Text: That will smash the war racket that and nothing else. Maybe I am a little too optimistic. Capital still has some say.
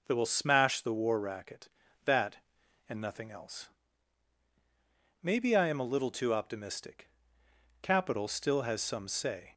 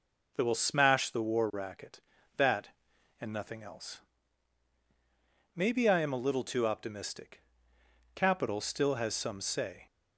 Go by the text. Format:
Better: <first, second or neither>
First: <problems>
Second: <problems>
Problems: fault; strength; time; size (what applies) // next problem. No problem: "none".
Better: neither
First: none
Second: none